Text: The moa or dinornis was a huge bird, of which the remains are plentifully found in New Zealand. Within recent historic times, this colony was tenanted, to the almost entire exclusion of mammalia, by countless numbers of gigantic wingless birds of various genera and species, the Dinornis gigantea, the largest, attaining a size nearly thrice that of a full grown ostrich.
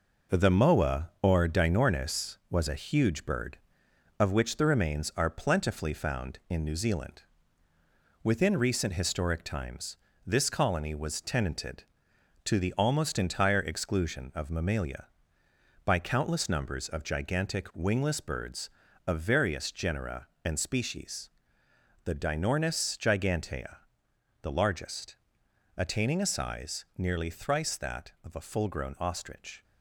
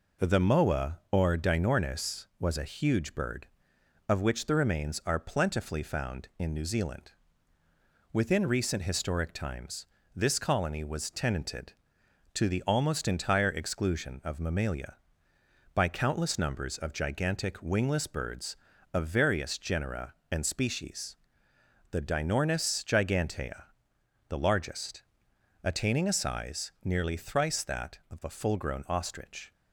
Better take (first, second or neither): second